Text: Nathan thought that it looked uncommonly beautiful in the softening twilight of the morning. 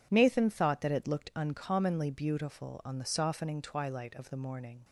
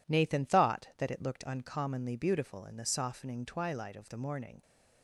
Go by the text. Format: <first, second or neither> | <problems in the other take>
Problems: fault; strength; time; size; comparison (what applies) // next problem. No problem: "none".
second | says "on" for "in"; at 2.8 s